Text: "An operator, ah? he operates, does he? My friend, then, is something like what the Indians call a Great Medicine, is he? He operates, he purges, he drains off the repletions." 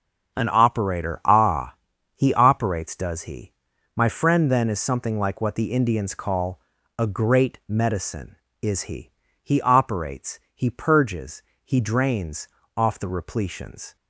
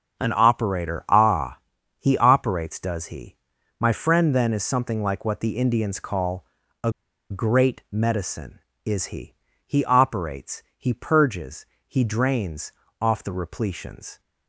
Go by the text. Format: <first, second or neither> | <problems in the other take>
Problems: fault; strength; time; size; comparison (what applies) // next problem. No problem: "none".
first | starts louder than the rest; until 1.2 s; 6.5 dB; also in the first // pauses between "call" and "a"; slight; at 6.4 s; 0.36 s long; slight in the first // pauses between "a" and "Great"; at 6.8 s; 0.40 s long // pauses between "drains" and "off"; slight; at 12.7 s; 0.28 s long; slight in the first